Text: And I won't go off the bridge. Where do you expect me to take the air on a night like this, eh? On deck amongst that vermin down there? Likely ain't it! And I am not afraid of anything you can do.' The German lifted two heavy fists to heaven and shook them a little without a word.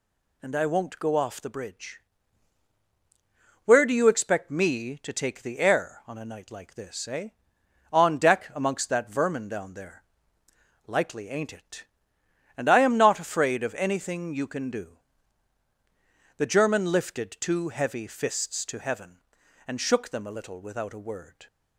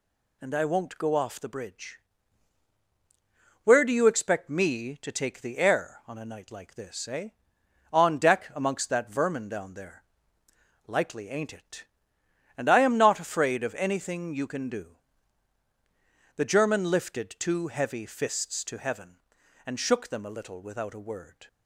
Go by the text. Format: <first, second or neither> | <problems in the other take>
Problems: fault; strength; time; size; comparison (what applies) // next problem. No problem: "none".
neither | none